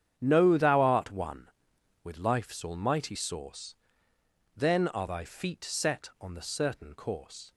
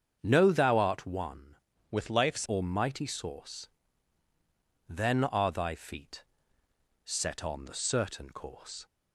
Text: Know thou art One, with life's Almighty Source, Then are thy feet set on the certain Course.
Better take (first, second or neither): first